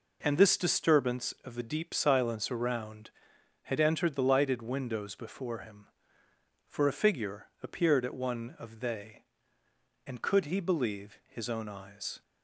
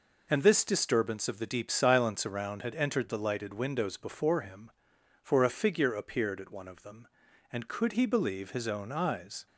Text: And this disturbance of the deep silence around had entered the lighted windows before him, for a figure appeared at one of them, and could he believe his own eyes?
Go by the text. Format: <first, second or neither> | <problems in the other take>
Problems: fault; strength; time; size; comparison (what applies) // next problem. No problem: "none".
second | pauses between "figure" and "appeared"; slight; at 7.4 s; 0.16 s long // says "they" for "them"; at 8.8 s